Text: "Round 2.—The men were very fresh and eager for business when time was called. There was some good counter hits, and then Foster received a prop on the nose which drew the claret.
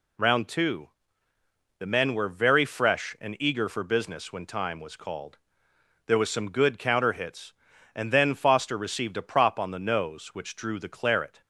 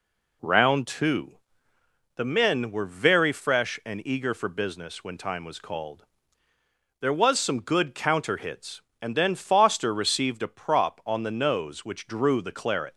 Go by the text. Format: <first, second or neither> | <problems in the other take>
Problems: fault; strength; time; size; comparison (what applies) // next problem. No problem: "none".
neither | none